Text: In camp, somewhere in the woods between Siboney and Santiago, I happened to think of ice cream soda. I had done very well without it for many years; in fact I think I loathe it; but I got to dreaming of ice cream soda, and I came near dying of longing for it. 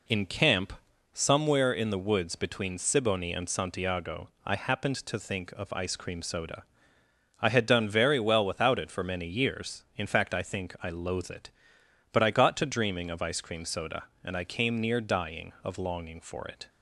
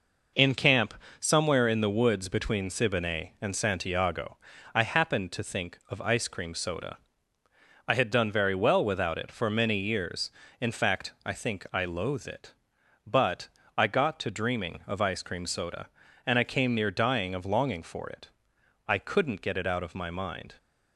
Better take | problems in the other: first | pauses between "but" and "I"; slight; at 13.4 s; 0.32 s long // goes on to say "I couldn't get it out of my mind"; from 18.8 s on; 1.6 s long

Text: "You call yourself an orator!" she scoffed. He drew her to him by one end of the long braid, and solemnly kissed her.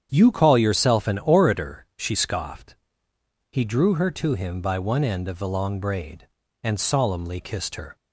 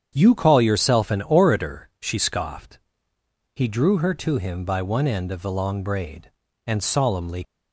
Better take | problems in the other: first | starts louder than the rest; strong; until 1.1 s; 8 dB; strong in the first // stops before "kissed her"; at 7.4 s

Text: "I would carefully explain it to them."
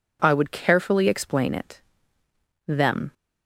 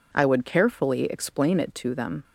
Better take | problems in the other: second | skips "to"; at 2.2 s

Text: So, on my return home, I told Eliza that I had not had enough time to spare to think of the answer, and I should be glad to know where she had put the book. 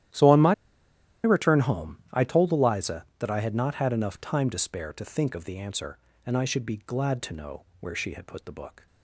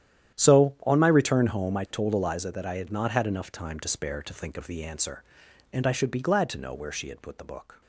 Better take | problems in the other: second | starts louder than the rest; strong; until 1.8 s; 12.5 dB; strong in the second // pauses between "my" and "return"; noticeable; at 0.5 s; 0.69 s long // pauses between "know" and "where"; slight; at 7.6 s; 0.16 s long

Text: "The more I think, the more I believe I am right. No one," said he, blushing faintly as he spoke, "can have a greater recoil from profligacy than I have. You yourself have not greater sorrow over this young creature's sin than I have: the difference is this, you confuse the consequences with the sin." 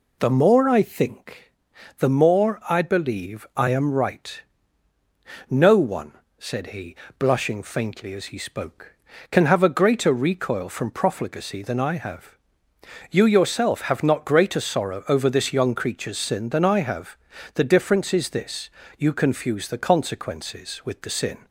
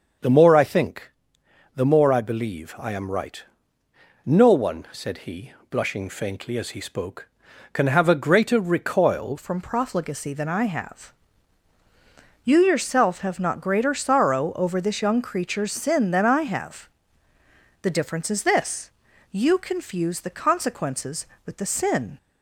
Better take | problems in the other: first | starts louder than the rest; until 1.8 s; 6.5 dB // changes voice at "from"; from 9.3 s on; 12.8 s long

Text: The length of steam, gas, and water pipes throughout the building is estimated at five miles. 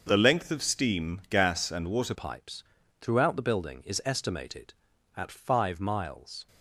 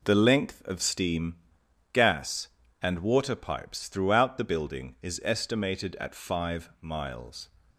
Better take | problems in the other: second | starts louder than the rest; until 1.0 s; 6.5 dB // changes voice at "pipes"; from 2.1 s on; 4.3 s long // pauses between "pipes" and "throughout"; slight; at 2.6 s; 0.36 s long

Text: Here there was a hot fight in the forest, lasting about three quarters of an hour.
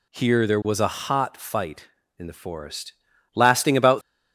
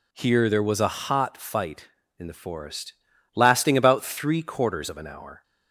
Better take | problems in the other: second | stops before "three quarters of an hour"; at 4.0 s

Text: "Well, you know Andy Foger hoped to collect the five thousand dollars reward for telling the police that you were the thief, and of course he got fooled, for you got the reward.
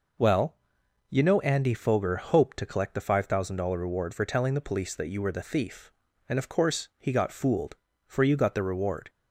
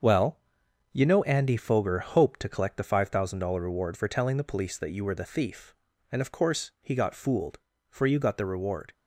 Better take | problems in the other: first | gets quieter; throughout; 7 dB

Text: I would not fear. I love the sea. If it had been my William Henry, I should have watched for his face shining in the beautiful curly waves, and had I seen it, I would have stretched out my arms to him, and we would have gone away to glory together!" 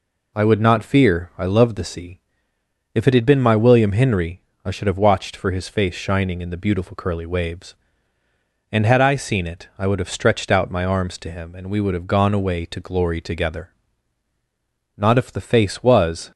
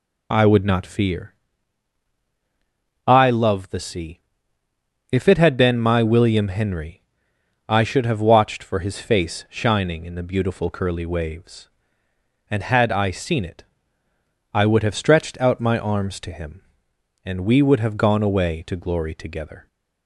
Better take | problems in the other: second | goes on to say "Not if the face was"; from 14.9 s on; 1.3 s long

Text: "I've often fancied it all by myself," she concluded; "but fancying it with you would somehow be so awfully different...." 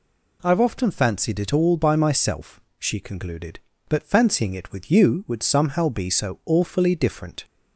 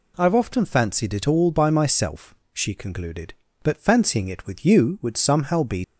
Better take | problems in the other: first | stops before "so awfully different"; at 5.8 s

